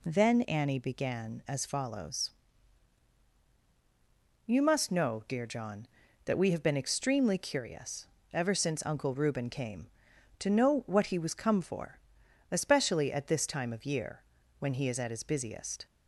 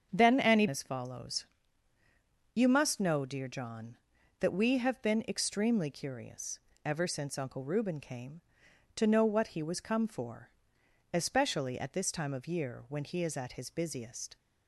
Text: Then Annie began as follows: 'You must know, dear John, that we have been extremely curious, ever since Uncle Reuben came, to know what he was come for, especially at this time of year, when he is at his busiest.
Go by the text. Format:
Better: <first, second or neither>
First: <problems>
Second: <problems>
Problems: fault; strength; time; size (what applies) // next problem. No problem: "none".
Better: first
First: none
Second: starts louder than the rest; strong; until 1.1 s; 7.5 dB // skips "began"; at 0.6 s